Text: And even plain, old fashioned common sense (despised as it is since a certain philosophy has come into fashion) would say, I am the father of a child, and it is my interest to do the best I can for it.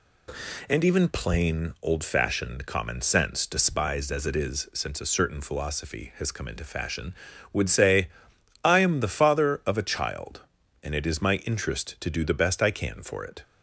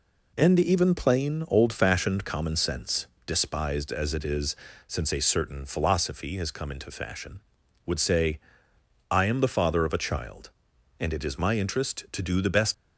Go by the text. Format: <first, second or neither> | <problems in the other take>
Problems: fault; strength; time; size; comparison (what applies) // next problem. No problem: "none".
first | pauses between "is" and "since"; slight; at 4.5 s; 0.32 s long // stops before "I can for it"; at 12.7 s